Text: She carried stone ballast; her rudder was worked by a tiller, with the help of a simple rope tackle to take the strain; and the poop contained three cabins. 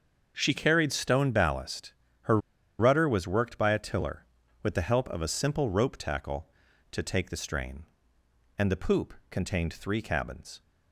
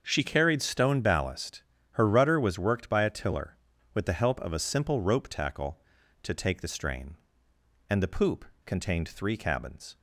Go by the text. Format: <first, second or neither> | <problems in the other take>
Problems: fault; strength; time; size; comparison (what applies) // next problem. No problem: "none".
second | starts louder than the rest; until 1.3 s; 6.5 dB; also in the second // pauses between "her" and "rudder"; at 2.3 s; 0.41 s long // pauses between "poop" and "contained"; slight; at 9.1 s; 0.16 s long; slight in the second